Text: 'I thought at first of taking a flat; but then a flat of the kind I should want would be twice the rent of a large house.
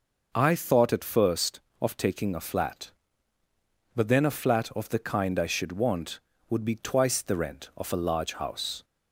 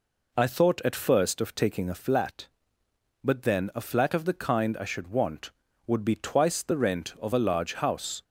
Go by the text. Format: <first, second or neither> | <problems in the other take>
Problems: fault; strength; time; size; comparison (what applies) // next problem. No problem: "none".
neither | none